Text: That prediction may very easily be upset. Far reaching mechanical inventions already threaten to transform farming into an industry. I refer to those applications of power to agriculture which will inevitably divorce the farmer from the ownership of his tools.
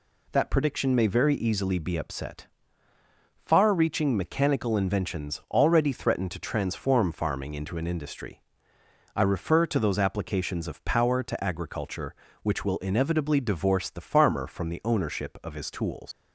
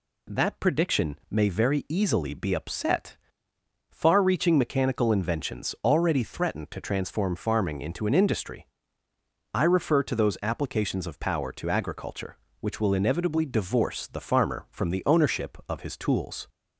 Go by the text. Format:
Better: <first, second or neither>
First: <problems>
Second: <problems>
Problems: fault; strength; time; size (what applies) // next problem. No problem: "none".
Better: second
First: leaves "tools" unfinished; at 16.1 s; 90 ms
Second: none